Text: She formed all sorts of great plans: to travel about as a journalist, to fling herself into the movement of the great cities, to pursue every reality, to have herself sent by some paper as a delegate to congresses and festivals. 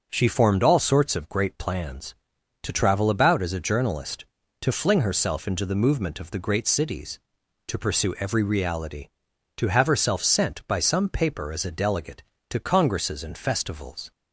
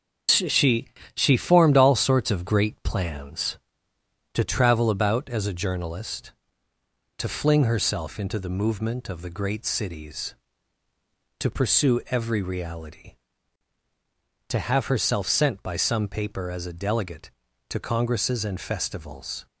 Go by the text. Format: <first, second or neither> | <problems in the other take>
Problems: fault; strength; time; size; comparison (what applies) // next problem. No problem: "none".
first | starts louder than the rest; until 1.5 s; 7 dB; noticeable in the first // says "She" twice; at 1.1 s